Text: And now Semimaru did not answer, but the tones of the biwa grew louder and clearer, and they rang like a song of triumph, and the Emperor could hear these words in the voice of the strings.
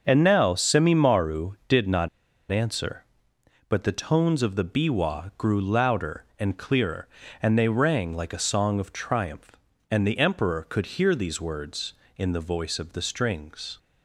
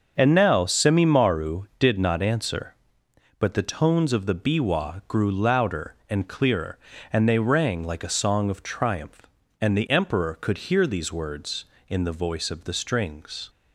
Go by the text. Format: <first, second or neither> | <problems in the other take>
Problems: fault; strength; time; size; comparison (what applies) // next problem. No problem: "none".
second | starts louder than the rest; until 1.0 s; 6.5 dB; also in the second // pauses between "not" and "answer"; at 2.0 s; 0.43 s long